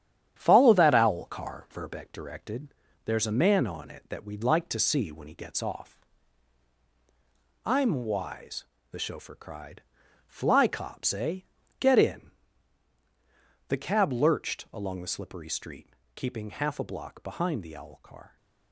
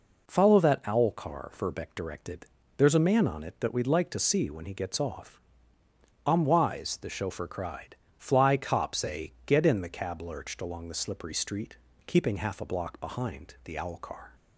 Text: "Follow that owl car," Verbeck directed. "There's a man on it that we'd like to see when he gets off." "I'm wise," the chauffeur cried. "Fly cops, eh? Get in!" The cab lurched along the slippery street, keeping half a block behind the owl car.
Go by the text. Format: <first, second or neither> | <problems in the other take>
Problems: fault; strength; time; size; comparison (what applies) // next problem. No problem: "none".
second | gets quieter; noticeable; throughout; 5.5 dB